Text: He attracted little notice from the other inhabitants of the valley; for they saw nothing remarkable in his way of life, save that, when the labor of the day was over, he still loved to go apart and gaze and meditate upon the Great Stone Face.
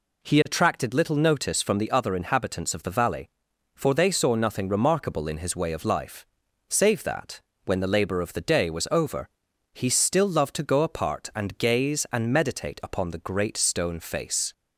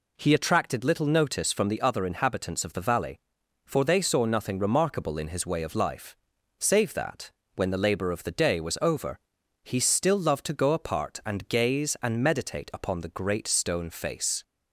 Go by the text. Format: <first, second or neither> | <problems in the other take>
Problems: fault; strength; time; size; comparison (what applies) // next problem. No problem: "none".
neither | none